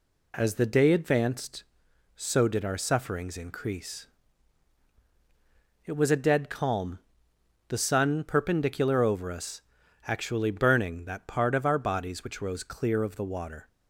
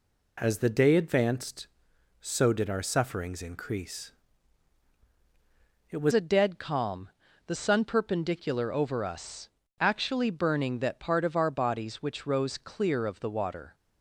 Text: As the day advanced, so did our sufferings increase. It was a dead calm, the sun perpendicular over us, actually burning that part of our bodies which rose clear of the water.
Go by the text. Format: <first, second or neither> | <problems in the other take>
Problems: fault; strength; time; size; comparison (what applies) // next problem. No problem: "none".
first | changes voice at "a"; from 6.1 s on; 7.6 s long